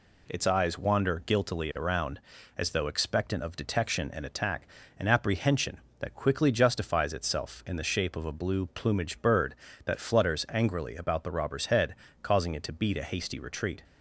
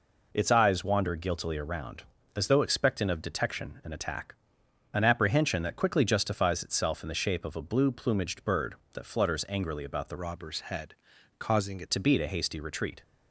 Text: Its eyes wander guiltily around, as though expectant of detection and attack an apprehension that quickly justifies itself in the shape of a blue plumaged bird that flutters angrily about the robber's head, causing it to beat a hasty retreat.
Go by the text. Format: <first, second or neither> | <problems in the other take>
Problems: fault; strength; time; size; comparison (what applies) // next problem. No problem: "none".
first | pauses between "attack" and "an"; noticeable; at 4.3 s; 0.58 s long; slight in the first // changes voice from "robber's" to "it"; from 10.1 to 11.9 s; 1.8 s long